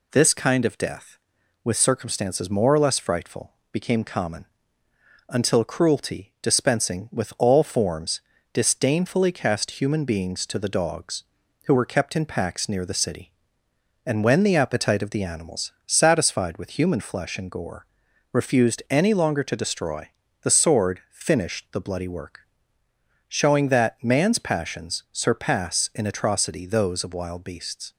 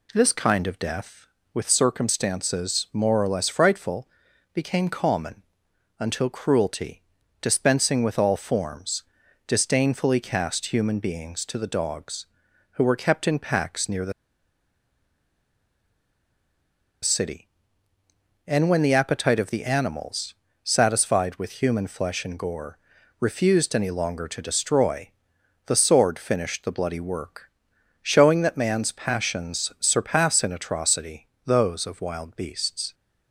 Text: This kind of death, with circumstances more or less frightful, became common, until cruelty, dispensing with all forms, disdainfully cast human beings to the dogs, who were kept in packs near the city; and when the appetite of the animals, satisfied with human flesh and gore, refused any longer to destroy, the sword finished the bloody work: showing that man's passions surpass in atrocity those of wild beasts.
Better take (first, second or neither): first